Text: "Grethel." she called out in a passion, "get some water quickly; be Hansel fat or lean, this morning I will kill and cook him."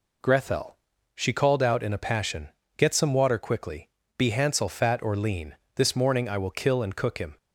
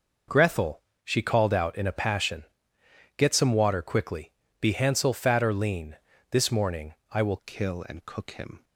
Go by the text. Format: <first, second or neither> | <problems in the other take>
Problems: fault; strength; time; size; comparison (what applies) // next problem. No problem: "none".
first | pauses between "morning" and "I"; slight; at 6.9 s; 0.18 s long // changes voice at "kill"; from 7.4 s on; 1.2 s long